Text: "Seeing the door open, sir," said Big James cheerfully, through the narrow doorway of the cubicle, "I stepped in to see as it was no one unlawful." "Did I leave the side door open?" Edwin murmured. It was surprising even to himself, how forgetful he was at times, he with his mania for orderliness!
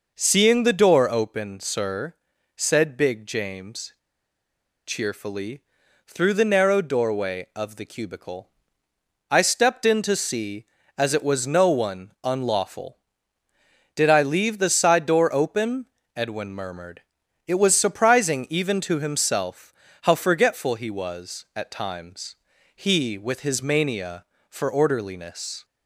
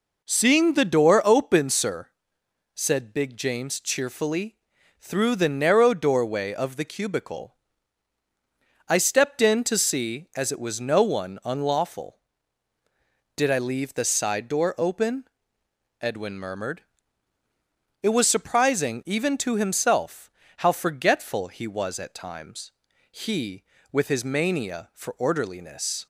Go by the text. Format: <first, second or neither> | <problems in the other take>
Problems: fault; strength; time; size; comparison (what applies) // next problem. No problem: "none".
second | pauses between "James" and "cheerfully"; noticeable; at 3.9 s; 0.92 s long